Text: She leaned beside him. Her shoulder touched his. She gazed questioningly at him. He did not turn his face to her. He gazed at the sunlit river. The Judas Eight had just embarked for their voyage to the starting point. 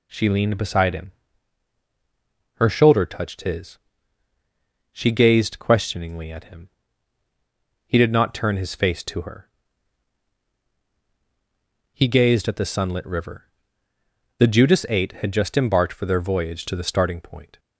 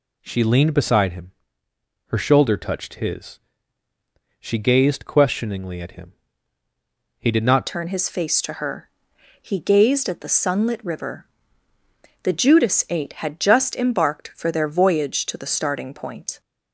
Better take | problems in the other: first | changes voice at "turn"; from 7.6 s on; 8.8 s long

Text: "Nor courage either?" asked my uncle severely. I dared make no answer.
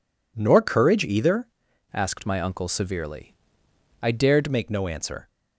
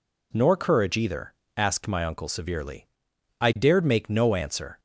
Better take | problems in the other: second | changes voice from "asked" to "dared"; from 1.9 to 4.4 s; 2.5 s long

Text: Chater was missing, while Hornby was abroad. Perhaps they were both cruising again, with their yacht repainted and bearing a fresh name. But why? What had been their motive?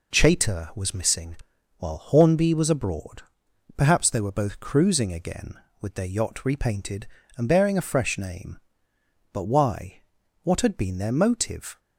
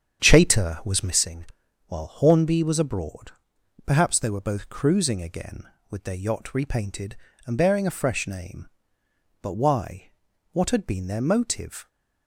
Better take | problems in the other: first | starts louder than the rest; strong; until 1.2 s; 8.5 dB

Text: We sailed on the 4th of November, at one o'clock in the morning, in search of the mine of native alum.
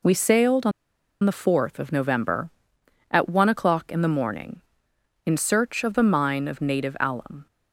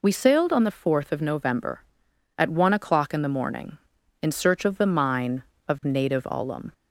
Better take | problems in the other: second | pauses between "on" and "the"; noticeable; at 0.7 s; 0.52 s long

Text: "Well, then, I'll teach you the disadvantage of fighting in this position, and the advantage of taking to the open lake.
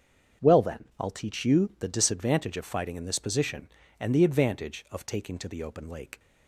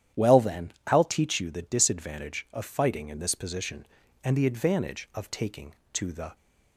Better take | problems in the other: first | starts louder than the rest; strong; until 1.3 s; 10.5 dB; also in the first // stops before "open lake"; at 6.3 s

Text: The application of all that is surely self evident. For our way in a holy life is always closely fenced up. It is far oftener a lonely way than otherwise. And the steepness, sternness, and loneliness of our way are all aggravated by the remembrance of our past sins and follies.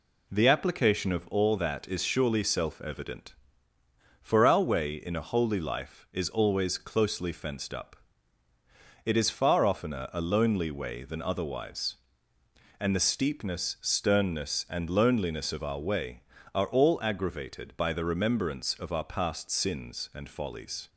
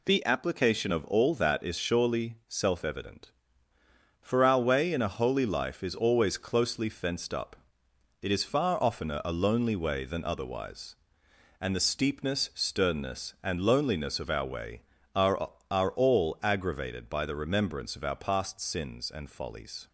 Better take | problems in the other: first | says "are" twice; at 15.7 s

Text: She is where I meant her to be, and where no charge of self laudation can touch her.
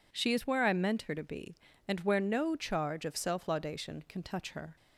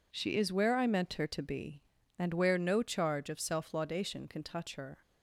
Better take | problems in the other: neither | none

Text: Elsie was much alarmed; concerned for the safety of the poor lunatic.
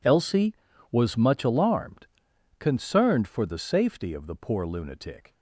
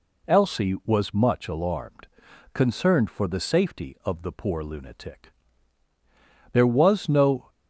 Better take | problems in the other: first | goes on to say "There was no"; noticeable; from 6.5 s on; 0.96 s long

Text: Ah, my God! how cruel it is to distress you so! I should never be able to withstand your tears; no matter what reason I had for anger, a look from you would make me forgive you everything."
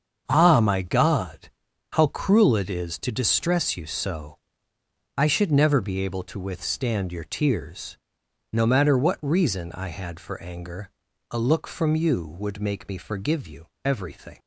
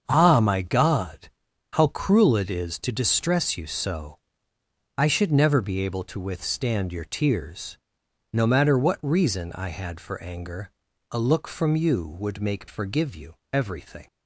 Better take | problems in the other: first | starts louder than the rest; strong; until 1.0 s; 7 dB; strong in the first // skips "me"; at 12.6 s // pauses between "you" and "everything"; slight; at 13.3 s; 0.18 s long; slight in the first

